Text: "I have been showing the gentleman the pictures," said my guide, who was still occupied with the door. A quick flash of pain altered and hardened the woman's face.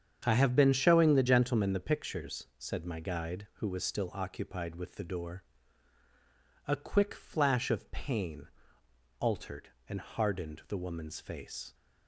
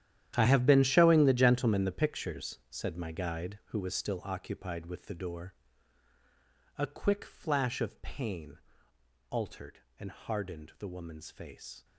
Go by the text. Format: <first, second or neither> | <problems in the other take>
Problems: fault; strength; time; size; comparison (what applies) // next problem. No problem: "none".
first | gets quieter; strong; throughout; 15 dB // starts louder than the rest; strong; until 1.3 s; 11 dB; strong in the first // pauses between "pain" and "altered"; noticeable; at 8.5 s; 0.72 s long; noticeable in the first